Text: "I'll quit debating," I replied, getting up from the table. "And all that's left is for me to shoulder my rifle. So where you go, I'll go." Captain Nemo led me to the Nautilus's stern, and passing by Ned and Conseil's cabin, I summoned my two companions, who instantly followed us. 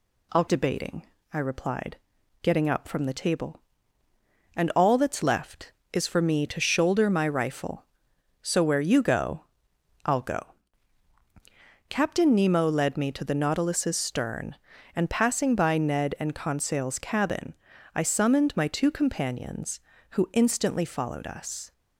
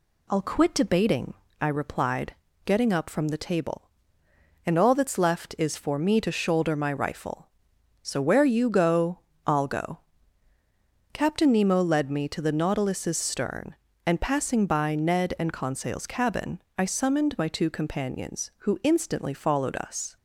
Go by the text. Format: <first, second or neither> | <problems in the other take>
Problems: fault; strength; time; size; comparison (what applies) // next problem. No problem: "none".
second | skips "quit"; at 0.4 s